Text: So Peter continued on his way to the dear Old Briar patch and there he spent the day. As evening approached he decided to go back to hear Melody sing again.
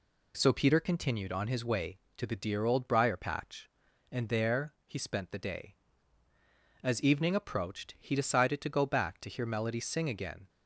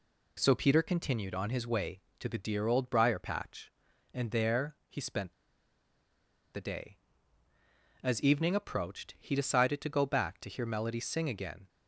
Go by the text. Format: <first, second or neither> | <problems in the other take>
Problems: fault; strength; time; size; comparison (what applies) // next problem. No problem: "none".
first | pauses between "spent" and "the"; at 5.3 s; 1.2 s long